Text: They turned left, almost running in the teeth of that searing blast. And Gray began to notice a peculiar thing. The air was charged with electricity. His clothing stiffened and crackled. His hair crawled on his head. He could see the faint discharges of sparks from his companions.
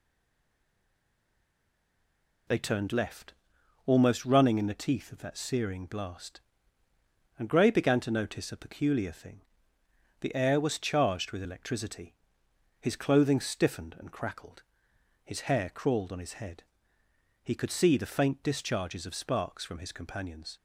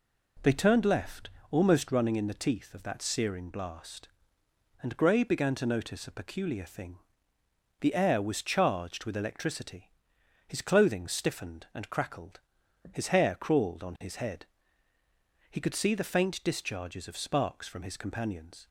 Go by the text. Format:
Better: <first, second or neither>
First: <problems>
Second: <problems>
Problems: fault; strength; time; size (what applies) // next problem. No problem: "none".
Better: second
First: stays silent before the first word; until 2.4 s; 2.4 s long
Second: none